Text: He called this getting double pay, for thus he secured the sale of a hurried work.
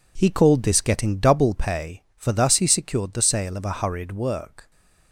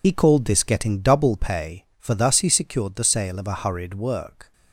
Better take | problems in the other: first | loses the start of "He"; at 0.0 s; 75 ms

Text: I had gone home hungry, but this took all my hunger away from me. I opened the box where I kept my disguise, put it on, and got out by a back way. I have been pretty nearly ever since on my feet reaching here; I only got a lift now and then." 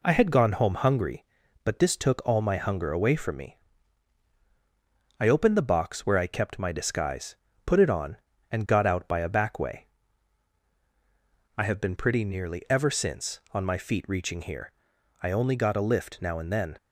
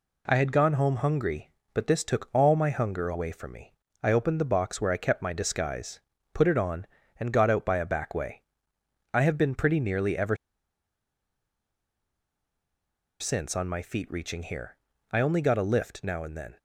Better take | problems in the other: first | pauses between "ever" and "since"; strong; at 10.3 s; 2.8 s long

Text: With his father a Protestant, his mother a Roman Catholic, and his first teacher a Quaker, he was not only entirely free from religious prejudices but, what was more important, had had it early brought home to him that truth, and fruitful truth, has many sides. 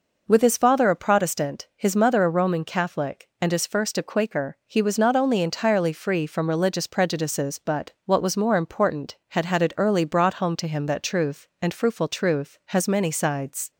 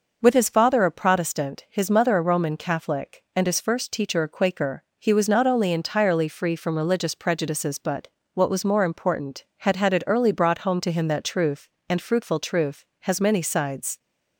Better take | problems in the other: second | skips "teacher"; at 3.9 s

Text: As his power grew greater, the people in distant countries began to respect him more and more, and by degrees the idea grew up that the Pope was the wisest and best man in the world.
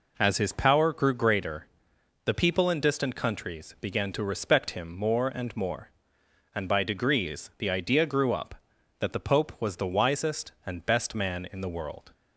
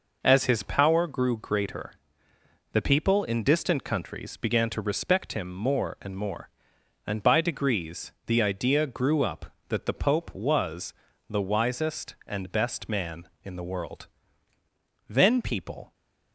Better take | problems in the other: first | pauses between "degrees" and "the"; slight; at 8.1 s; 0.16 s long // pauses between "was" and "the"; slight; at 10.9 s; 0.36 s long // goes on to say "Then people"; noticeable; from 15.0 s on; 0.84 s long

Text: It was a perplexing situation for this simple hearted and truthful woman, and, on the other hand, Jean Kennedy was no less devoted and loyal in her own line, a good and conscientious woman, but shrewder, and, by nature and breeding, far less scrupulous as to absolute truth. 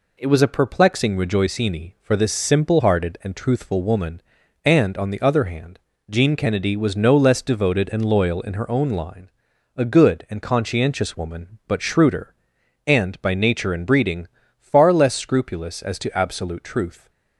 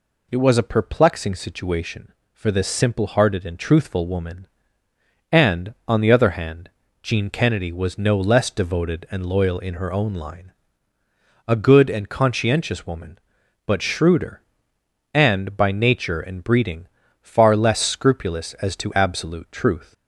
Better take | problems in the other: second | says "rejoicini" for "situation"; at 1.1 s

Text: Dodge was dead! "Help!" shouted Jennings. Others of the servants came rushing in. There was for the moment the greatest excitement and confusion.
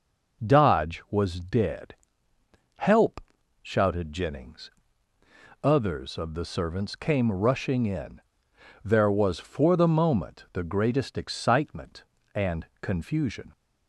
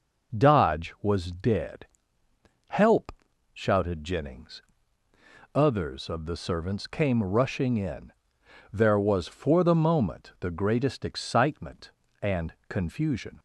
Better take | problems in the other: neither | none

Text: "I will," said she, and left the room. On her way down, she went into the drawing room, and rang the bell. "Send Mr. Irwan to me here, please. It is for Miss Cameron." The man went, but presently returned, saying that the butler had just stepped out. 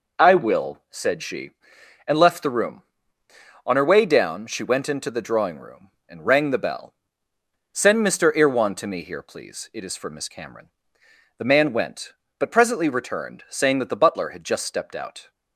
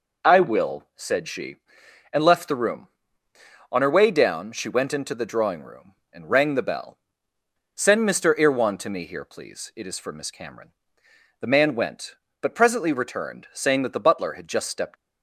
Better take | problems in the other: first | stops before "out"; at 14.9 s

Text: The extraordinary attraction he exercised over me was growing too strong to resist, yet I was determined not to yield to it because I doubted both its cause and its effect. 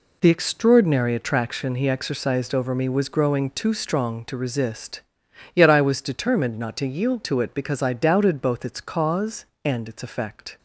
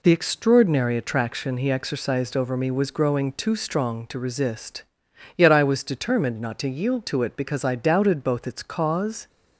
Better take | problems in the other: first | stops before "and its effect"; at 9.2 s

